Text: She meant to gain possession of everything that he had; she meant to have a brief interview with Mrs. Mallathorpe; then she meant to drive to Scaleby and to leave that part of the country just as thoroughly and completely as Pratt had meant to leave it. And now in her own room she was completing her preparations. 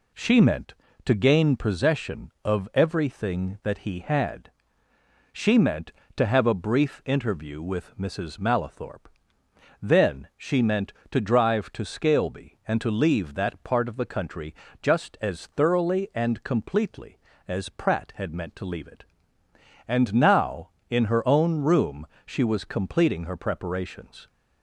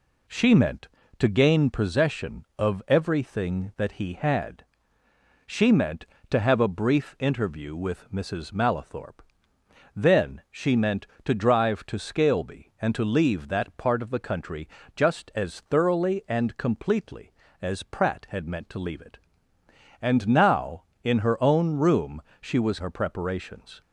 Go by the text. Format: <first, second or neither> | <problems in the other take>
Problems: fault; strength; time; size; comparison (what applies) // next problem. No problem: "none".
first | pauses between "country" and "just"; slight; at 14.6 s; 0.26 s long; slight in the first // pauses between "room" and "she"; slight; at 22.2 s; 0.22 s long; slight in the first // skips "completing"; at 22.7 s